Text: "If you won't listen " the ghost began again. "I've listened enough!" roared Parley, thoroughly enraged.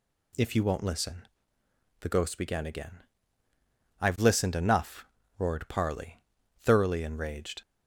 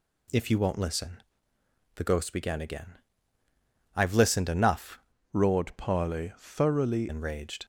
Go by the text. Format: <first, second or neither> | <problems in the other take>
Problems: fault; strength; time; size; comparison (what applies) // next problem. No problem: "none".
first | changes voice from "roared" to "thoroughly"; from 5.3 to 7.0 s; 1.7 s long